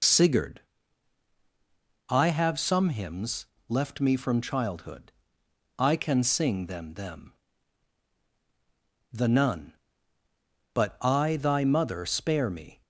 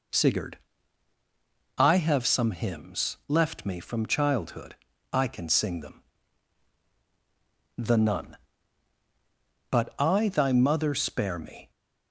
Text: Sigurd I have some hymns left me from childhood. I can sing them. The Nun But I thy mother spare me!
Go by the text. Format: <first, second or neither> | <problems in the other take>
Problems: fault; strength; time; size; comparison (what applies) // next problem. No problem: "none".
second | pauses between "Sigurd" and "I"; strong; at 0.5 s; 1.5 s long; also in the second // pauses between "hymns" and "left"; slight; at 3.4 s; 0.24 s long // says "them" twice; at 6.9 s